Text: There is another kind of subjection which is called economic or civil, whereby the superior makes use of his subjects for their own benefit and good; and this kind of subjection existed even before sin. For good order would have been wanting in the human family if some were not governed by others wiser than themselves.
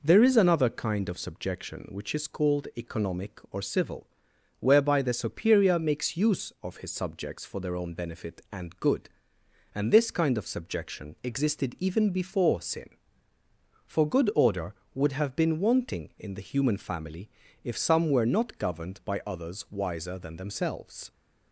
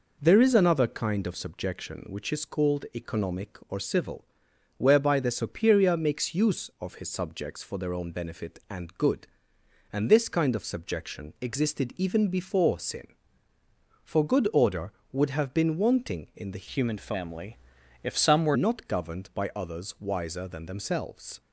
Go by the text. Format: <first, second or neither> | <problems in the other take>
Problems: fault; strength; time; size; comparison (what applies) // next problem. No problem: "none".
first | changes voice from "human" to "were"; from 16.7 to 18.5 s; 1.8 s long // pauses between "family" and "if"; noticeable; at 17.5 s; 0.48 s long; slight in the first